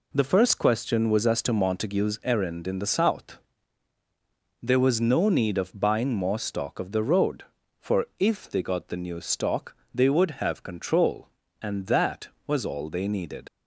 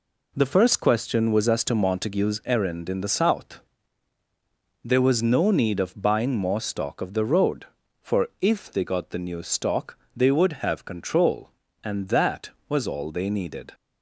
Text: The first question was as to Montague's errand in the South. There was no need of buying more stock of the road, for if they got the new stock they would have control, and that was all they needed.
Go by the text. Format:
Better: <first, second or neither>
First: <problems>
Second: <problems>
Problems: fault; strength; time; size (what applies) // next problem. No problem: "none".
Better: second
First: pauses between "stock" and "they"; slight; at 9.7 s; 0.16 s long // leaves "needed" unfinished; at 13.4 s; 40 ms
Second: pauses between "stock" and "they"; slight; at 9.9 s; 0.16 s long